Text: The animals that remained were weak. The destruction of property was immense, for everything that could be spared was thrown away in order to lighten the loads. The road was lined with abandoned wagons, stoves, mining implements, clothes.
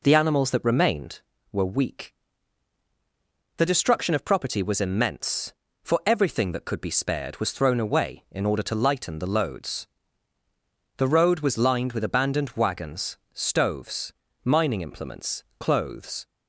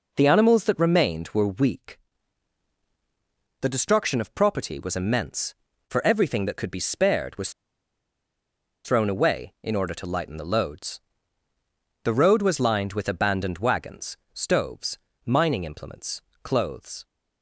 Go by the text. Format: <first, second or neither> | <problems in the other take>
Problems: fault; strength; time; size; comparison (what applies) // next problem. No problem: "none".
first | pauses between "was" and "thrown"; strong; at 7.5 s; 1.3 s long